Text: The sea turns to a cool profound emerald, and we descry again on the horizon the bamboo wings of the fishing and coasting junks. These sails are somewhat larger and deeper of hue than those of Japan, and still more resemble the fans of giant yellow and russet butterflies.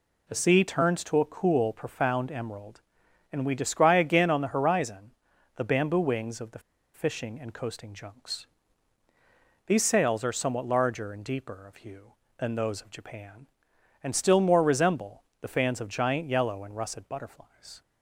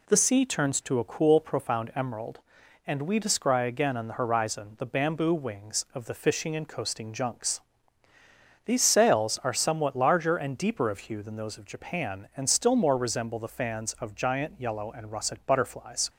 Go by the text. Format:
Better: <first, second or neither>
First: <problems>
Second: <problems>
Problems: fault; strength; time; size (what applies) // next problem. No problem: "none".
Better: second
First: pauses between "horizon" and "the"; at 5.1 s; 0.44 s long // pauses between "the" and "fishing"; slight; at 6.5 s; 0.35 s long // pauses between "resemble" and "the"; slight; at 15.2 s; 0.18 s long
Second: none